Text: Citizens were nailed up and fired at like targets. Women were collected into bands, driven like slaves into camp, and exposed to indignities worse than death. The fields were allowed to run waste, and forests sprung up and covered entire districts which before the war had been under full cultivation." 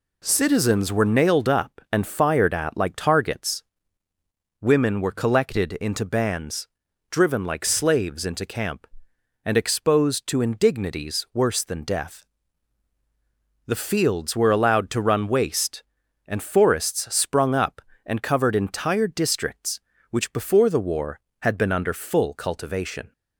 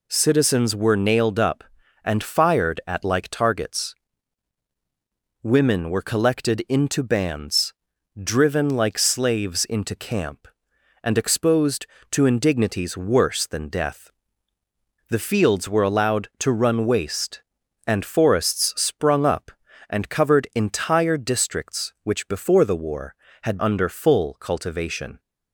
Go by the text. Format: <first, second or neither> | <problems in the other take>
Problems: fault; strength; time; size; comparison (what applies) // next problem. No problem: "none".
first | skips "been"; at 23.5 s